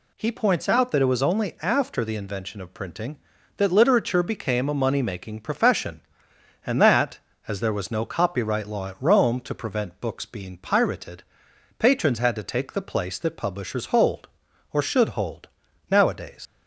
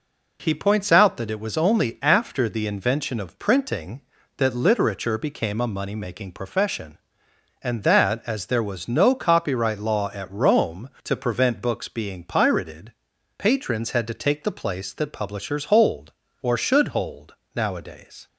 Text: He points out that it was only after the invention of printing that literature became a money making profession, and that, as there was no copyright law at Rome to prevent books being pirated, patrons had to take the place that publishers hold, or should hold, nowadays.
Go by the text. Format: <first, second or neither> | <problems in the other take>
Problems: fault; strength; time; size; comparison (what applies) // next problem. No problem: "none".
second | leaves "nowadays" unfinished; at 16.4 s; 80 ms